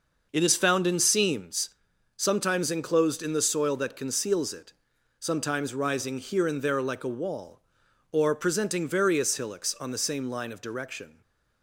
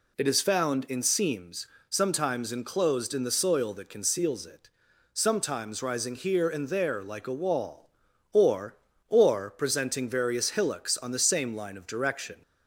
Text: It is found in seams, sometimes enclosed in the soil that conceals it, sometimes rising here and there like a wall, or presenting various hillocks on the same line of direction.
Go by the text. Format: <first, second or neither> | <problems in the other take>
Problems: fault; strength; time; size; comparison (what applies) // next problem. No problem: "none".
first | says "or" twice; at 9.0 s